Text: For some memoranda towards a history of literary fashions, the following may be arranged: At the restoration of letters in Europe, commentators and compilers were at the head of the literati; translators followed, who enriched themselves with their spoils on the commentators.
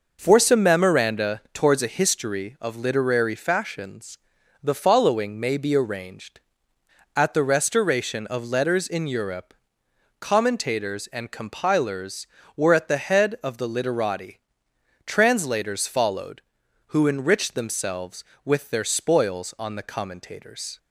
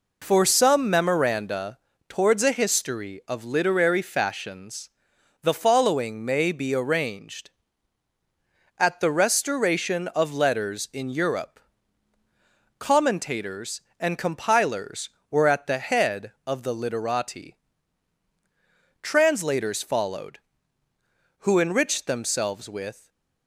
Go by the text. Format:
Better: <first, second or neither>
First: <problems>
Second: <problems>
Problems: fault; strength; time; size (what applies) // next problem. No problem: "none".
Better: first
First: none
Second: pauses between "memoranda" and "towards"; slight; at 1.7 s; 0.28 s long // stops before "their spoils on the commentators"; at 23.0 s